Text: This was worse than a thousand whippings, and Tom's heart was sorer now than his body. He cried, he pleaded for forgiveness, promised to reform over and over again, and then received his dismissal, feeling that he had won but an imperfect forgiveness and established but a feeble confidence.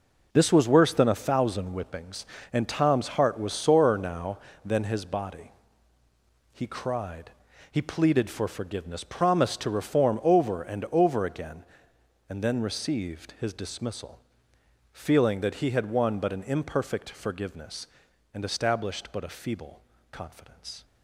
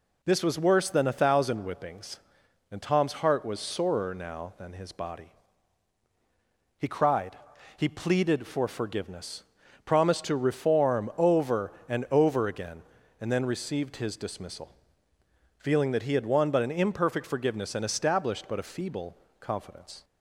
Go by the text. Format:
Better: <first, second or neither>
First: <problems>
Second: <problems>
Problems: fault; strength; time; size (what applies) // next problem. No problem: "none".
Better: second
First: gets quieter; strong; throughout; 10 dB // pauses between "feeble" and "confidence"; slight; at 19.8 s; 0.32 s long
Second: pauses between "feeble" and "confidence"; slight; at 19.1 s; 0.24 s long